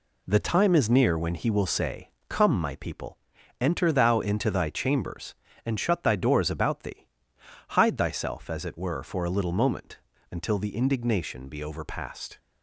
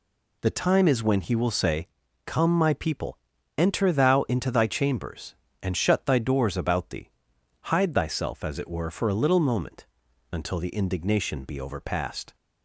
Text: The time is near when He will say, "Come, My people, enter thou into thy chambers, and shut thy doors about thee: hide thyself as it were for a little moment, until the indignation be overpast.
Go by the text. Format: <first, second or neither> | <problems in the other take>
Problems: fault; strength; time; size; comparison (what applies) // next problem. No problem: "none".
first | skips "near"; at 1.0 s